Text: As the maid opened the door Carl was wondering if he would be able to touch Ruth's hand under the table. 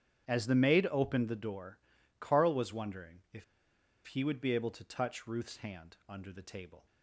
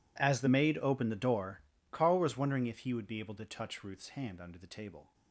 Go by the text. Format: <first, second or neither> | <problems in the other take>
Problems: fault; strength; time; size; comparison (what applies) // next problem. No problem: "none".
second | starts louder than the rest; strong; until 1.3 s; 9.5 dB // pauses between "door" and "Carl"; at 1.7 s; 0.42 s long; slight in the second // pauses between "if" and "he"; noticeable; at 3.4 s; 0.63 s long